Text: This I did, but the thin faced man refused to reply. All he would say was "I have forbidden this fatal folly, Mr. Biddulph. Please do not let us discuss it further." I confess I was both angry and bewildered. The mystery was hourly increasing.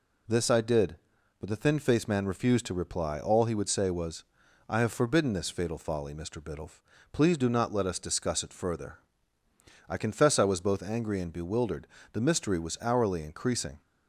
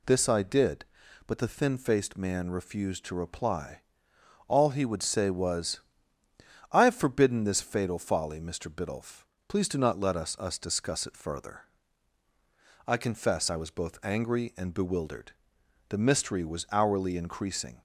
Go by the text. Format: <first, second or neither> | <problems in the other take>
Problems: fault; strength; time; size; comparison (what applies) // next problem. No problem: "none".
first | pauses between "was" and "I"; noticeable; at 5.7 s; 0.94 s long; also in the first // says "us" twice; at 10.3 s